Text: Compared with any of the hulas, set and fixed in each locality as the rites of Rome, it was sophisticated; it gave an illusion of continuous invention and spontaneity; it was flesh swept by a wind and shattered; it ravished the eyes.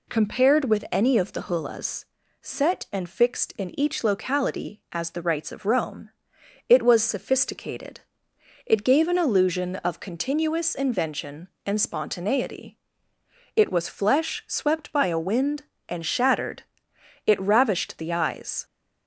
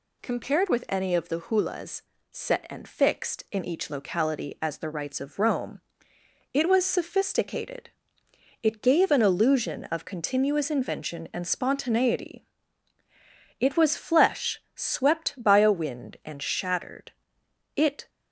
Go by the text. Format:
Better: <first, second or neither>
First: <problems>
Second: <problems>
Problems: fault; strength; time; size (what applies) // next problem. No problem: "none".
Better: first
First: none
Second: stops before "ravished the eyes"; at 18.0 s